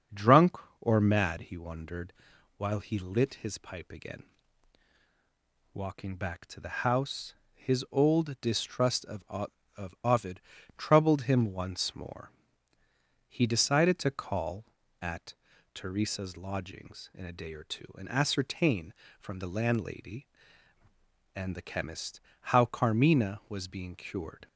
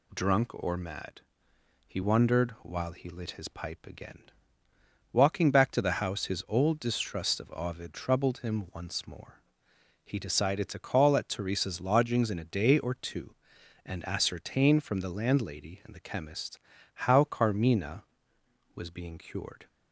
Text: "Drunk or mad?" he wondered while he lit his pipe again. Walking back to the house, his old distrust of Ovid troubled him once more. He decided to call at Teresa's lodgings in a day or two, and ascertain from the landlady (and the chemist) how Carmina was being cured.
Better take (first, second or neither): second